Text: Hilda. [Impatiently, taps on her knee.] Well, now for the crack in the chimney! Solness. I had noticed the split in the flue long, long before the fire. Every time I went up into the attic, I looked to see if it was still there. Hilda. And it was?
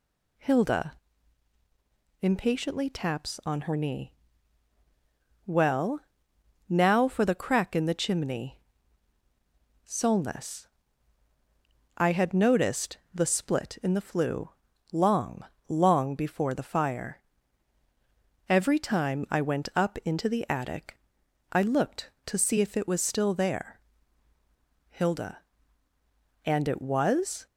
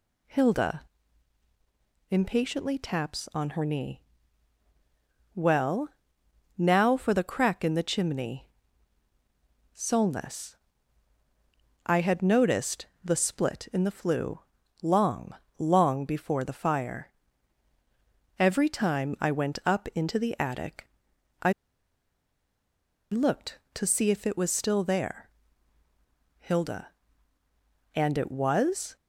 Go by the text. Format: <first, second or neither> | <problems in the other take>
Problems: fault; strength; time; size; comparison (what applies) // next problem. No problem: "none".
first | pauses between "noticed" and "the"; slight; at 12.8 s; 0.16 s long // pauses between "flue" and "long"; at 14.3 s; 0.42 s long; also in the first // pauses between "I" and "looked"; strong; at 21.5 s; 1.6 s long